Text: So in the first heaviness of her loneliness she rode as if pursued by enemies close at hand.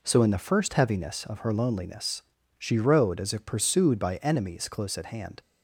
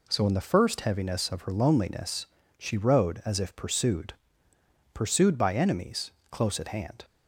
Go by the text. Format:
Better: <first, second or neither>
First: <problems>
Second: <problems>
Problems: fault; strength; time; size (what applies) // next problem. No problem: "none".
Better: first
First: pauses between "loneliness" and "she"; slight; at 2.2 s; 0.34 s long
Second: pauses between "loneliness" and "she"; slight; at 2.2 s; 0.32 s long // says "pursued" twice; at 4.9 s // pauses between "enemies" and "close"; slight; at 6.1 s; 0.20 s long